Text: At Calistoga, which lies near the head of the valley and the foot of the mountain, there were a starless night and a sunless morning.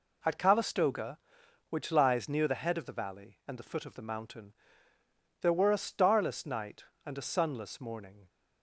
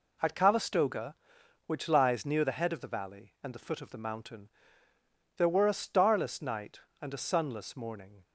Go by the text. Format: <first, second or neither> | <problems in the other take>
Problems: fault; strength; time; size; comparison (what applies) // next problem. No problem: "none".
neither | none